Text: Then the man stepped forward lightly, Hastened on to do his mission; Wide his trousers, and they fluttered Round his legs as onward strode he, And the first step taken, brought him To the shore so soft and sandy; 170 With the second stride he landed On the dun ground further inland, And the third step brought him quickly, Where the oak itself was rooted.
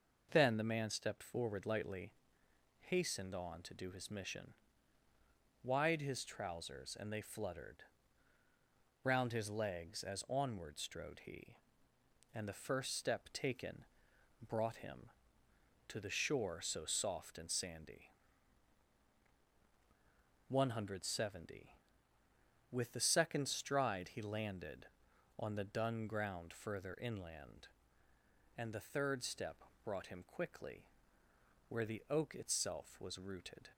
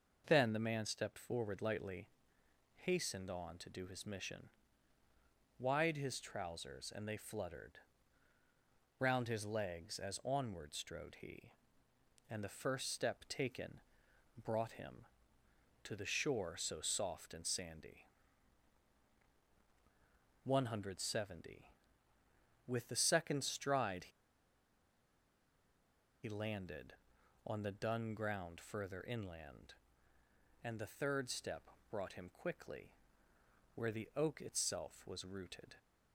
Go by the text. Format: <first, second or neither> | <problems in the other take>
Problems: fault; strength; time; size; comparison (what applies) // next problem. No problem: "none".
first | pauses between "fluttered" and "Round"; at 7.7 s; 1.2 s long; also in the first // pauses between "stride" and "he"; strong; at 24.0 s; 2.1 s long // pauses between "step" and "brought"; slight; at 31.6 s; 0.20 s long; slight in the first